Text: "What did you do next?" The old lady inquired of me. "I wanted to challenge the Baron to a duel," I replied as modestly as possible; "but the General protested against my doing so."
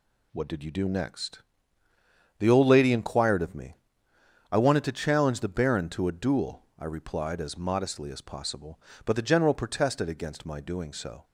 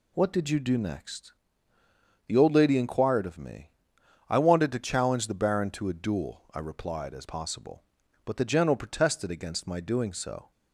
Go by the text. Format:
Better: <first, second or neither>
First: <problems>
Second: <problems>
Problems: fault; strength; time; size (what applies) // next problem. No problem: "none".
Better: first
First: none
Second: skips "modestly as"; at 7.2 s